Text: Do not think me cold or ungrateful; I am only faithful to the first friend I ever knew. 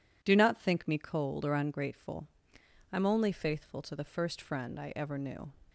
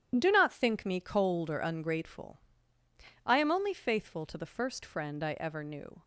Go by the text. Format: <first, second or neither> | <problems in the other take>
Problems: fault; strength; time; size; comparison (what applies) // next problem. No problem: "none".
neither | none